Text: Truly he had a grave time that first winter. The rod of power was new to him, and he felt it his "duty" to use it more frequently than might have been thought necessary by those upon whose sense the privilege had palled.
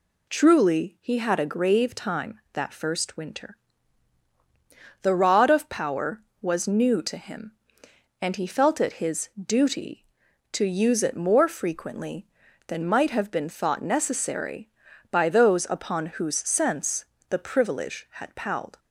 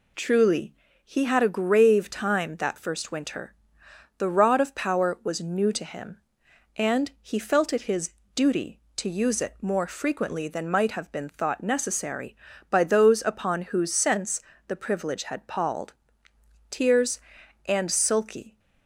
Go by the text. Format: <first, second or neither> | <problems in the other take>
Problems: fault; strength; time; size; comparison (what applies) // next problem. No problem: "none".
first | pauses between "Truly" and "he"; slight; at 0.7 s; 0.30 s long // pauses between "his" and "duty"; slight; at 8.1 s; 0.22 s long // pauses between "sense" and "the"; slight; at 14.3 s; 0.28 s long; slight in the first // goes on to say "Tears and sulky"; strong; from 16.6 s on; 1.9 s long